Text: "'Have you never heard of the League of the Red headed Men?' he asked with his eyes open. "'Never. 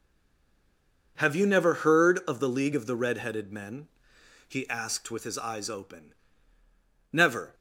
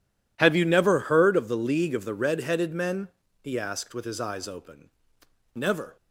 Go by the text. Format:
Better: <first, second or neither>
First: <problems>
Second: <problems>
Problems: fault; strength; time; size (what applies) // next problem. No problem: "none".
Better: second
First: stays silent before the first word; until 1.1 s; 1.1 s long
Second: none